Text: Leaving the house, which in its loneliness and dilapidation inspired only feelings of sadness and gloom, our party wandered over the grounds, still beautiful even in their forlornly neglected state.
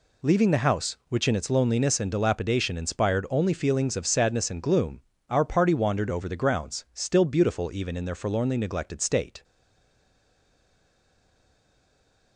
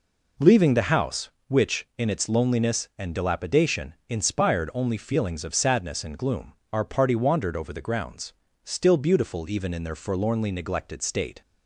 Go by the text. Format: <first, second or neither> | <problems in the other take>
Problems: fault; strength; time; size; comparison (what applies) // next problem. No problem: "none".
second | stays silent after the last word; strong; from 9.4 s on; 2.9 s long